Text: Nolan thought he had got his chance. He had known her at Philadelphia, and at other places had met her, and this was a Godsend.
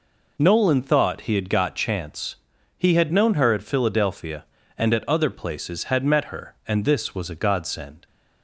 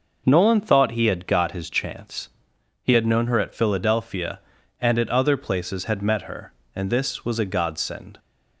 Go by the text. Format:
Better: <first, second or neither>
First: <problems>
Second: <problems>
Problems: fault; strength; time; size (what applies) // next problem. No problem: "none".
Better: second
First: skips "his"; at 1.7 s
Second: none